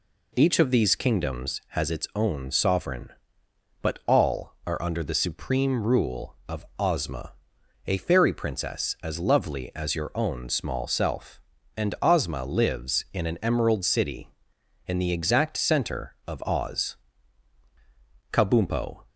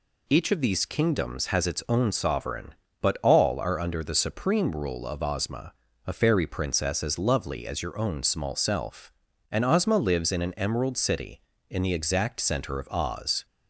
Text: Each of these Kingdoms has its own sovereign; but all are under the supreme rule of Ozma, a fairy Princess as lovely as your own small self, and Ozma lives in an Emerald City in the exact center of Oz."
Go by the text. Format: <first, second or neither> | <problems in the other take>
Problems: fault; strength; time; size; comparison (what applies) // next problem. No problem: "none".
second | goes on to say "Kabumpo"; noticeable; from 18.3 s on; 0.72 s long